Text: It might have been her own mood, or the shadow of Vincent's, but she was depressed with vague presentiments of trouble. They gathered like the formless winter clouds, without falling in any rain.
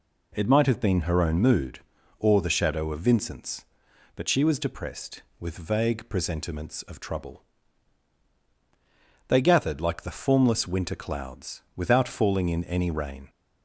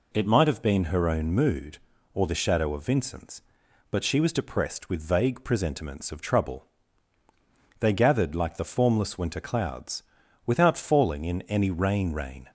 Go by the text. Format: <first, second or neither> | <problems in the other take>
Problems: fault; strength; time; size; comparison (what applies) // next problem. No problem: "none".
first | says "rain" twice; at 12.1 s